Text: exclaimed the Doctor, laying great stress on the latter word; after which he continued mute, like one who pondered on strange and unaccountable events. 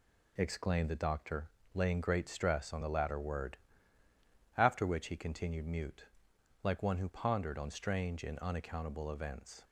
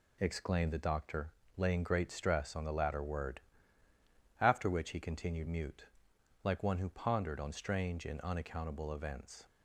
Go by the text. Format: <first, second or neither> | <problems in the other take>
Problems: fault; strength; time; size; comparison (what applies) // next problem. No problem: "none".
neither | none